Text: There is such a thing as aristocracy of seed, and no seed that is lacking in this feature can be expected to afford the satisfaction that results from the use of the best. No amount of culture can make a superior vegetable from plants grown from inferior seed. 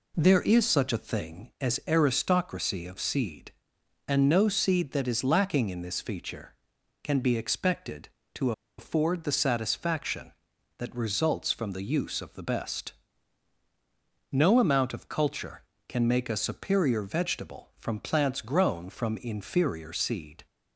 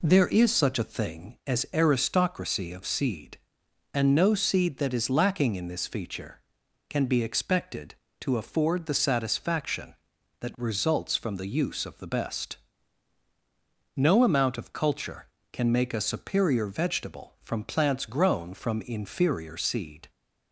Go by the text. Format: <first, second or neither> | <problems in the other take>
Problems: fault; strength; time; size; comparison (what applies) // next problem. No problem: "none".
second | pauses between "to" and "afford"; slight; at 8.5 s; 0.26 s long